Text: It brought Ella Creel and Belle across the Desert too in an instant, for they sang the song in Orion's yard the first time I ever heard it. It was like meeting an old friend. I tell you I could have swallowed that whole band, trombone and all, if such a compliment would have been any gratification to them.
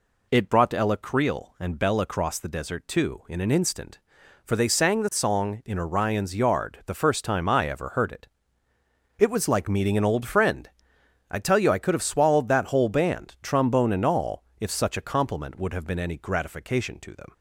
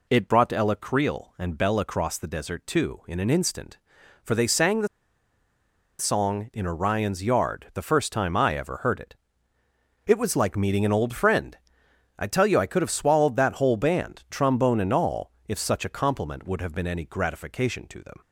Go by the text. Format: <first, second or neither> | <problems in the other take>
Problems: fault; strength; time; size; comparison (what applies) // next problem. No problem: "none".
first | pauses between "the" and "song"; at 4.8 s; 1.1 s long